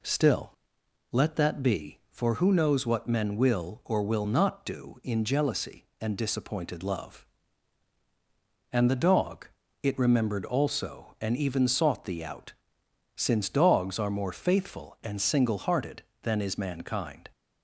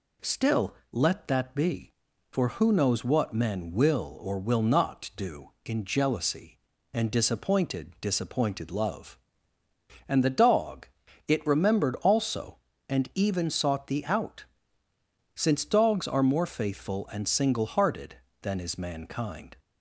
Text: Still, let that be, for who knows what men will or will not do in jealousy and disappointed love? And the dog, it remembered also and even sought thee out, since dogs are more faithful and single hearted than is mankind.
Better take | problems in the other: first | says "disappointed" twice; at 8.0 s

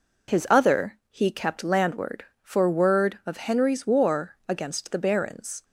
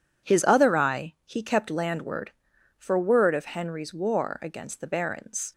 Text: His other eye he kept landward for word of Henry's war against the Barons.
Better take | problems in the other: second | skips "eye"; at 1.0 s

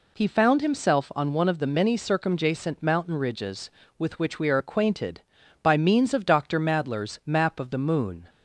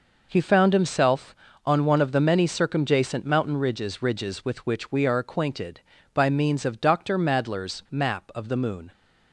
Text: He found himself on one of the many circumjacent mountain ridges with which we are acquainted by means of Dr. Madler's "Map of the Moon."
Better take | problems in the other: first | says "ridges" twice; at 3.9 s

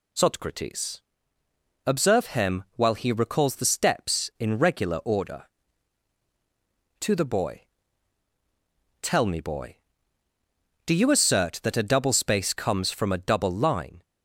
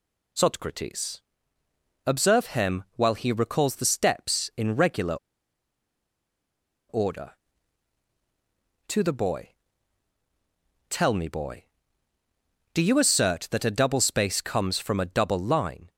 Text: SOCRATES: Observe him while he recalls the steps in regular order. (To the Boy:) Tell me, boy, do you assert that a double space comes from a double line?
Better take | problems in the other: first | pauses between "regular" and "order"; strong; at 5.1 s; 1.7 s long

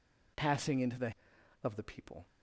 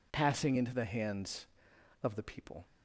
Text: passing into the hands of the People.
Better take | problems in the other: second | skips "hands"; at 1.3 s

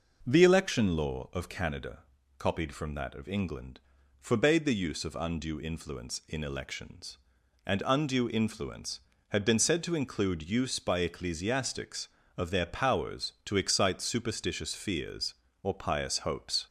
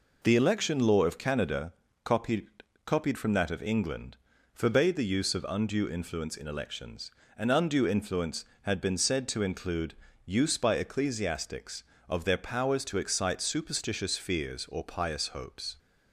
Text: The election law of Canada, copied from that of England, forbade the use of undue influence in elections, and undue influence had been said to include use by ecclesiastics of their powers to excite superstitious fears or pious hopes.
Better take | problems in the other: first | says "copied" twice; at 2.8 s // pauses between "include" and "use"; slight; at 9.9 s; 0.32 s long

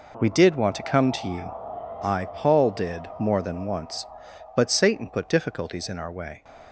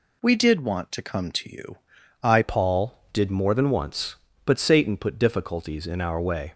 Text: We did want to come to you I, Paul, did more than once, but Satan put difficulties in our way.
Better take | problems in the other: first | pauses between "you" and "I"; at 1.7 s; 0.44 s long; noticeable in the first // changes voice at "Paul"; from 2.4 s on; 4.1 s long

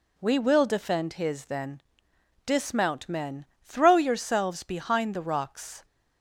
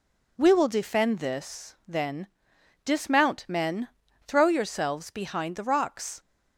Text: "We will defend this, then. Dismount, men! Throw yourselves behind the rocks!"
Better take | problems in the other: second | says "his" for "this"; at 1.1 s

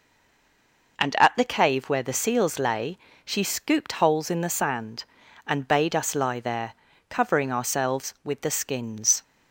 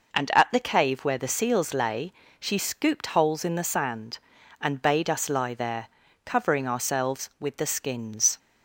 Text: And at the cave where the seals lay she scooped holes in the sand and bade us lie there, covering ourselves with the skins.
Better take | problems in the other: second | stays silent before the first word; until 0.9 s; 0.9 s long // pauses between "lay" and "she"; slight; at 2.9 s; 0.28 s long; slight in the second

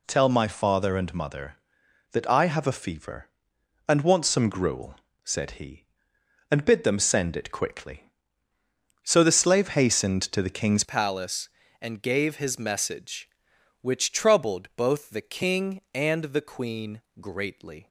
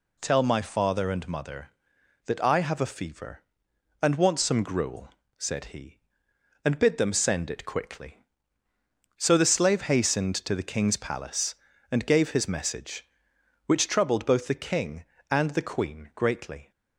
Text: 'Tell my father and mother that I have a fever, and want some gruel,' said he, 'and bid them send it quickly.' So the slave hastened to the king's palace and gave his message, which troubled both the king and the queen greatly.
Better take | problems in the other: second | changes voice at "palace"; from 10.8 s on; 7.0 s long // pauses between "queen" and "greatly"; slight; at 17.0 s; 0.18 s long

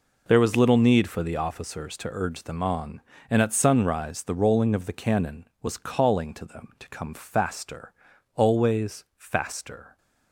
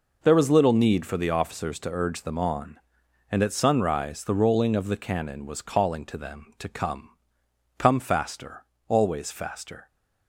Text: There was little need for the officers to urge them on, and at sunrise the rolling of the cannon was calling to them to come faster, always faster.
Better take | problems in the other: first | says "come" twice; at 7.7 s

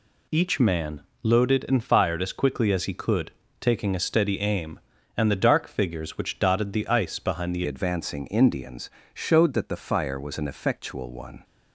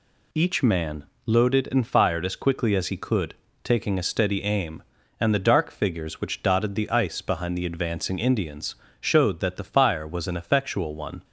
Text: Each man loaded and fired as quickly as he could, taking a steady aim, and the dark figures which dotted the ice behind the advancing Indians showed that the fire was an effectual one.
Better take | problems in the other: second | pauses between "man" and "loaded"; slight; at 1.0 s; 0.18 s long; slight in the second // changes voice at "advancing"; from 7.6 s on; 3.8 s long // pauses between "Indians" and "showed"; slight; at 8.9 s; 0.24 s long; slight in the second

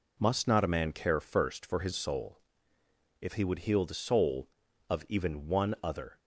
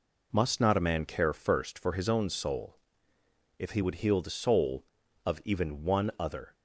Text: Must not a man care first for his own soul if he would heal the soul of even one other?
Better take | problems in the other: second | skips "own"; at 1.9 s // pauses between "soul" and "if"; noticeable; at 2.3 s; 0.82 s long; noticeable in the second

